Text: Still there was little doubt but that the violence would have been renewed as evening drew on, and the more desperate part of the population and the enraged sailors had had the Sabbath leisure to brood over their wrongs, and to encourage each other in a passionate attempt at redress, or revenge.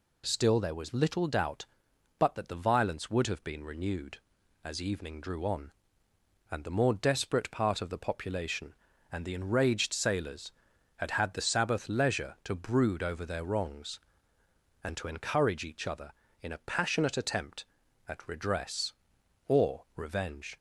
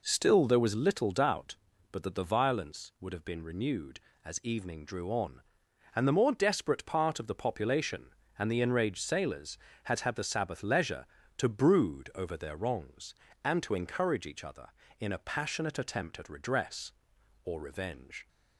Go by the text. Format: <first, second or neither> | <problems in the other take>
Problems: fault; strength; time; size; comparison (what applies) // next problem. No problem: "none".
neither | none